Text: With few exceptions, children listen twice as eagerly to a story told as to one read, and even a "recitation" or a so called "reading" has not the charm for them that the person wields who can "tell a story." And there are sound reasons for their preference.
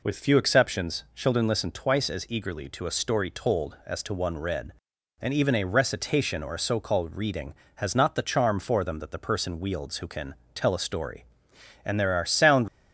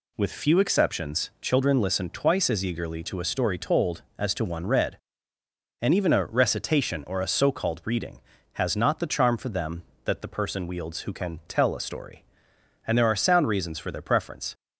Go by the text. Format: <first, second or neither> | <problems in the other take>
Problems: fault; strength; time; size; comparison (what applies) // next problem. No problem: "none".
second | pauses between "can" and "tell"; slight; at 10.3 s; 0.20 s long // stops before "reasons for their preference"; at 12.6 s